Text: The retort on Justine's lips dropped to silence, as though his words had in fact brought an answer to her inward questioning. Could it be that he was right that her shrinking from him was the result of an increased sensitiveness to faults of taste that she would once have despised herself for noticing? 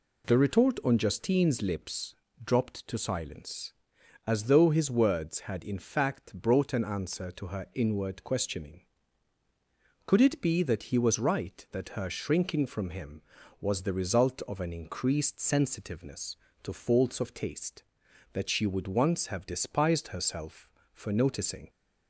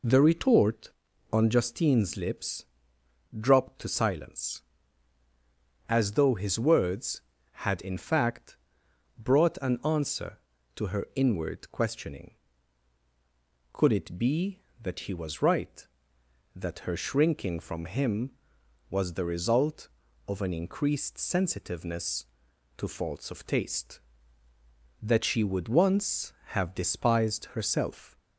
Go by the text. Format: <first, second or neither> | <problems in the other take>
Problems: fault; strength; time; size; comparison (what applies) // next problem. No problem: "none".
first | pauses between "lips" and "dropped"; noticeable; at 2.6 s; 0.70 s long; slight in the first // pauses between "fact" and "brought"; noticeable; at 8.5 s; 0.62 s long // stops before "for noticing"; at 28.1 s